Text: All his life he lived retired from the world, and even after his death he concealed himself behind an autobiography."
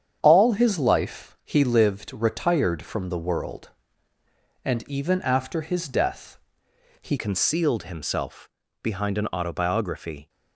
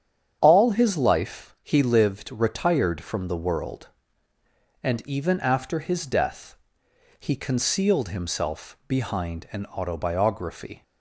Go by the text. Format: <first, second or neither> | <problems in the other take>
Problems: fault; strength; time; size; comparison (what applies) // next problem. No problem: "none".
second | starts louder than the rest; strong; until 1.2 s; 8.5 dB; strong in the second // pauses between "death" and "he"; noticeable; at 6.3 s; 0.64 s long; noticeable in the second // changes voice at "concealed"; from 7.1 s on; 3.1 s long // pauses between "himself" and "behind"; slight; at 8.4 s; 0.32 s long